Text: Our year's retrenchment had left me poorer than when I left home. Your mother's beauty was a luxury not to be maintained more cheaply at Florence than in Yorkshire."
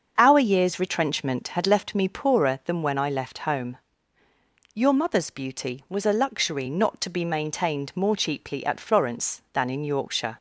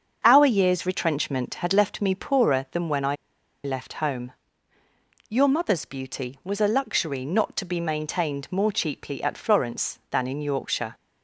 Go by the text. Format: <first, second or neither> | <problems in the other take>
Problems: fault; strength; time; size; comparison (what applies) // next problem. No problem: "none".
first | starts louder than the rest; until 1.2 s; 7 dB; also in the first // pauses between "I" and "left"; noticeable; at 3.1 s; 0.48 s long